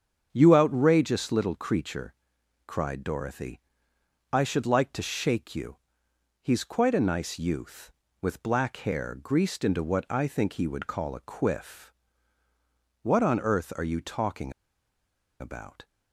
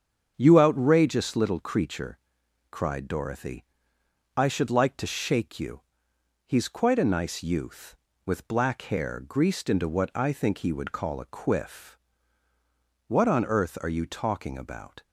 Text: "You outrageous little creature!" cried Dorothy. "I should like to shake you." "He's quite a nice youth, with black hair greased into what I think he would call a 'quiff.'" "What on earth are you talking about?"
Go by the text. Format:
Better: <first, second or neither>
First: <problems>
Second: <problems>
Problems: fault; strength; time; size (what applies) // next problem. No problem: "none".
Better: second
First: starts louder than the rest; strong; until 1.3 s; 7.5 dB // pauses between "talking" and "about"; noticeable; at 14.5 s; 0.88 s long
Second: starts louder than the rest; strong; until 1.3 s; 7.5 dB